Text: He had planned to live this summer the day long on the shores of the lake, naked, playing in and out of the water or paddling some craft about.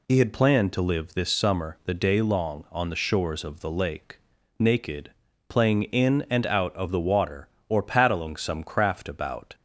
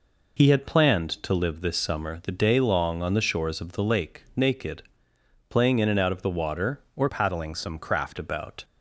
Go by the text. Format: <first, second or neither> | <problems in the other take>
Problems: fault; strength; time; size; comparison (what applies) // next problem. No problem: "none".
first | changes voice from "paddling" to "craft"; from 7.0 to 8.1 s; 1.1 s long